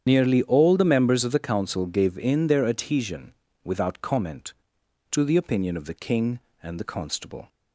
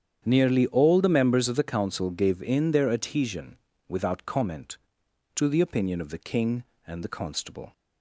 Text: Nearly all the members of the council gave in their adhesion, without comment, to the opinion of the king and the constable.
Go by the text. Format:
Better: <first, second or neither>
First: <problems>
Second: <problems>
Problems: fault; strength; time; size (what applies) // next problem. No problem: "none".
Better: second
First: loses the start of "Nearly"; at 0.0 s; 65 ms // starts louder than the rest; strong; until 1.0 s; 8.5 dB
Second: starts louder than the rest; strong; until 1.2 s; 8.5 dB